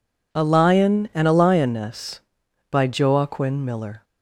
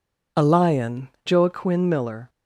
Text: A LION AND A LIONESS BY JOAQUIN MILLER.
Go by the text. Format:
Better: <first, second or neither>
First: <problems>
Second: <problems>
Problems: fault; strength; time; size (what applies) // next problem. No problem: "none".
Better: first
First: none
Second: skips "AND A LIONESS BY"; at 1.1 s